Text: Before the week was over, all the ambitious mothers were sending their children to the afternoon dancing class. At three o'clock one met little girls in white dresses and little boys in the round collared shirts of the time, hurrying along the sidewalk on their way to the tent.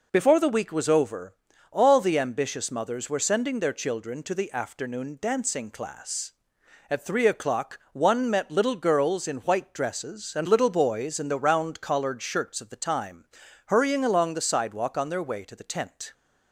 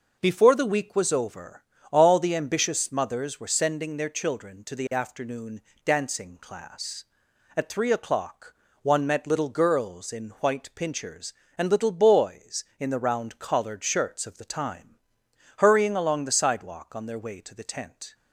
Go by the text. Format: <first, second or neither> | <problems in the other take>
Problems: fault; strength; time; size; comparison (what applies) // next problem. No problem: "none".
first | pauses between "afternoon" and "dancing"; slight; at 5.6 s; 0.22 s long // pauses between "o'clock" and "one"; slight; at 8.5 s; 0.30 s long // says "pinchers" for "dresses"; at 10.7 s